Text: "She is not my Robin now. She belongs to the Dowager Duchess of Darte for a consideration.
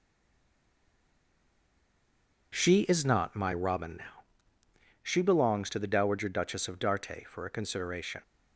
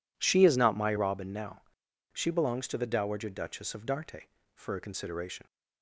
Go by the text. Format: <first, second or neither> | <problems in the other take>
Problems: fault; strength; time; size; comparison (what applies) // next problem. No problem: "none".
second | stays silent before the first word; until 2.5 s; 2.5 s long